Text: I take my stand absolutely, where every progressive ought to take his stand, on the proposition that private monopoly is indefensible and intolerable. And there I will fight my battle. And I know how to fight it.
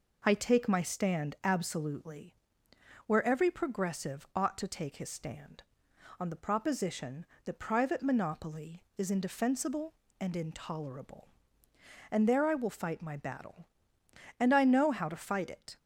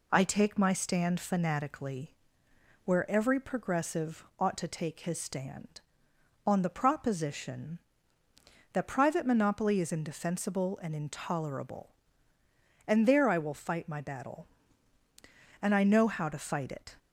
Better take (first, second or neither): first